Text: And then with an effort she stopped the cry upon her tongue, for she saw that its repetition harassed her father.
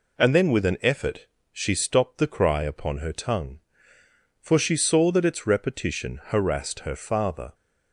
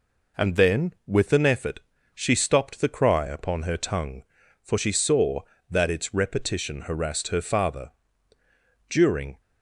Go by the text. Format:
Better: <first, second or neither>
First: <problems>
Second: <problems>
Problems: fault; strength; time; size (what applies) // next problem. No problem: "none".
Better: first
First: pauses between "effort" and "she"; slight; at 1.2 s; 0.26 s long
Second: pauses between "effort" and "she"; slight; at 1.8 s; 0.34 s long // goes on to say "During"; from 8.8 s on; 0.52 s long